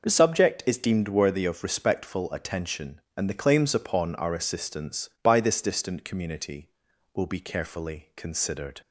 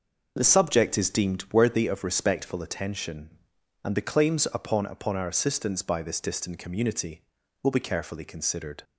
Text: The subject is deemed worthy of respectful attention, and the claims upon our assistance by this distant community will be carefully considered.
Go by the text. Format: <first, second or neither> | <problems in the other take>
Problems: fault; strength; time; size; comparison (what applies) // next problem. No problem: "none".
first | starts louder than the rest; noticeable; until 1.3 s; 6 dB // says "upon" twice; at 4.8 s